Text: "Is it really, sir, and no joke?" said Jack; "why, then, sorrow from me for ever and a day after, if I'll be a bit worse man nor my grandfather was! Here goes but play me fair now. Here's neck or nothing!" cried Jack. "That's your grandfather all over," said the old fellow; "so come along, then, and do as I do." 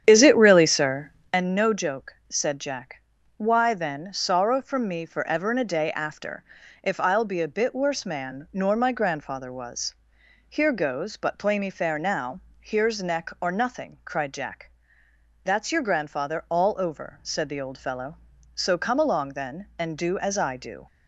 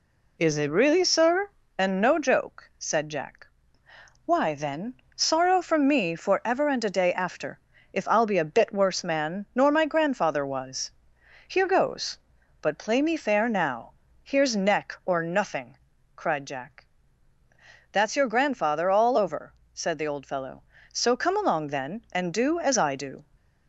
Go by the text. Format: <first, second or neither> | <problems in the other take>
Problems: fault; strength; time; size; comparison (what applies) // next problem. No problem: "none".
second | starts louder than the rest; strong; until 1.4 s; 9 dB